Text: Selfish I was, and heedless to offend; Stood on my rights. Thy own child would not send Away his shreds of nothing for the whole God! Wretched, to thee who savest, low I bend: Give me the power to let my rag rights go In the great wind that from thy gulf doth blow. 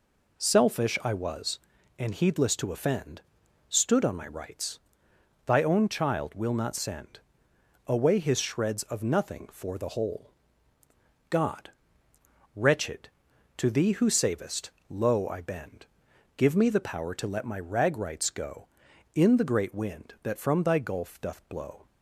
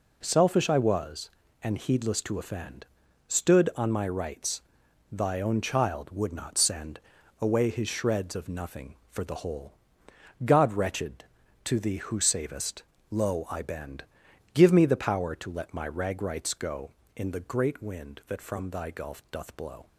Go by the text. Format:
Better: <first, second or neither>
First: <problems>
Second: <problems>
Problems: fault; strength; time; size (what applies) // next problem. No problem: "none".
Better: second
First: says "will" for "would"; at 6.3 s // pauses between "send" and "Away"; noticeable; at 7.1 s; 0.66 s long // pauses between "whole" and "God"; at 10.2 s; 1.0 s long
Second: pauses between "send" and "Away"; at 6.9 s; 0.40 s long // pauses between "whole" and "God"; noticeable; at 9.7 s; 0.72 s long